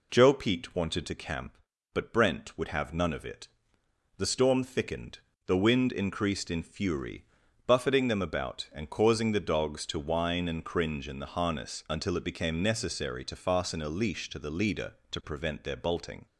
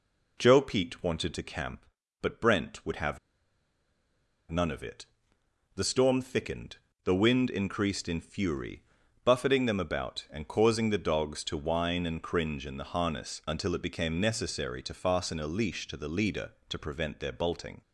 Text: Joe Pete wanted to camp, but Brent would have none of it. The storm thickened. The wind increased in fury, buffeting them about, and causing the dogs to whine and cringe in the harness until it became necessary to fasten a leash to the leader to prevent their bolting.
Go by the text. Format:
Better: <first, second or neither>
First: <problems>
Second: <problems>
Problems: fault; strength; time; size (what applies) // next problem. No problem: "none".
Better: first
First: none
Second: pauses between "have" and "none"; strong; at 3.1 s; 1.3 s long